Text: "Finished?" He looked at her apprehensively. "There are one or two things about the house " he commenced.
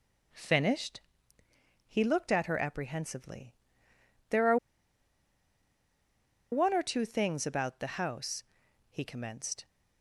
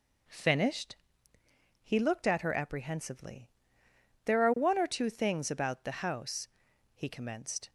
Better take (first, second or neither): second